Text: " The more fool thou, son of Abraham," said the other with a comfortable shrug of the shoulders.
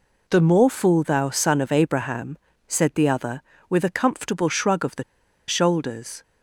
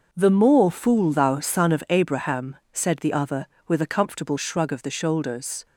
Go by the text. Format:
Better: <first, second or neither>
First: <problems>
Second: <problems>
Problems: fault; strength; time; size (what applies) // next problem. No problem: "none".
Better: second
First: pauses between "the" and "shoulders"; at 5.0 s; 0.44 s long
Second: none